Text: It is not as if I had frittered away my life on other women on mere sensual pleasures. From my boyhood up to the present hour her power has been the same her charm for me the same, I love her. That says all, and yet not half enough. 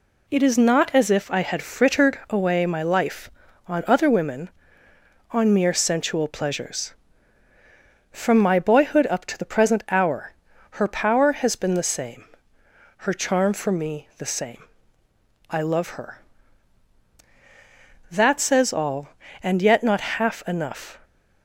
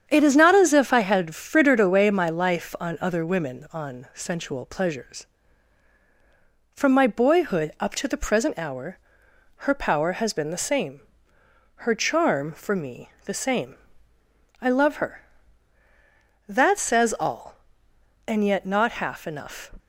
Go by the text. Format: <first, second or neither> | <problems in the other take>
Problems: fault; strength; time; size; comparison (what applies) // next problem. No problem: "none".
first | starts louder than the rest; strong; until 1.1 s; 8 dB // skips "mere"; at 4.0 s // pauses between "hour" and "her"; noticeable; at 8.9 s; 0.62 s long; also in the first // pauses between "same" and "her"; noticeable; at 11.0 s; 0.86 s long; noticeable in the first // pauses between "me" and "the"; slight; at 13.0 s; 0.16 s long